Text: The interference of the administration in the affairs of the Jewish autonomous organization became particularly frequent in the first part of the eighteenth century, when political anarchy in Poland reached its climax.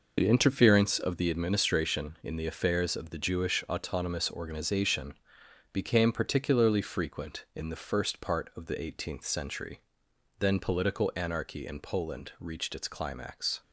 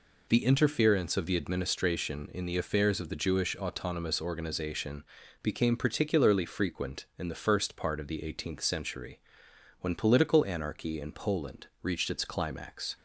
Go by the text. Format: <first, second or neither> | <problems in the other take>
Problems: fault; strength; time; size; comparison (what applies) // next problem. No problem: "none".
second | pauses between "organization" and "became"; noticeable; at 5.1 s; 0.58 s long; also in the second // says "then" for "when"; at 10.4 s